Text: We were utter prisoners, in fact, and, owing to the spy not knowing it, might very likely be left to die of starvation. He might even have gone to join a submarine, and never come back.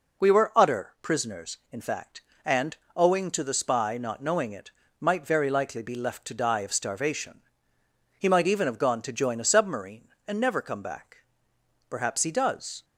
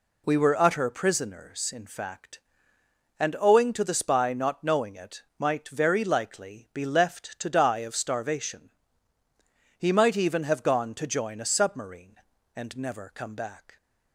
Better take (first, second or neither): second